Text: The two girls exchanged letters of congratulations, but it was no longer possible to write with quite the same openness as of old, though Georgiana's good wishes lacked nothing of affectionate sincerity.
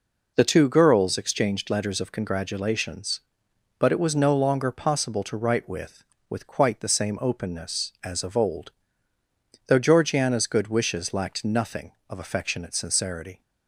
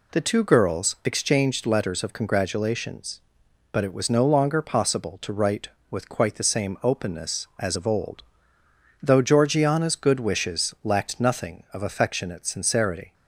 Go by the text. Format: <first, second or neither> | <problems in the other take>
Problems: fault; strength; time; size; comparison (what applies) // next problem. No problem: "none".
second | says "with" twice; at 6.2 s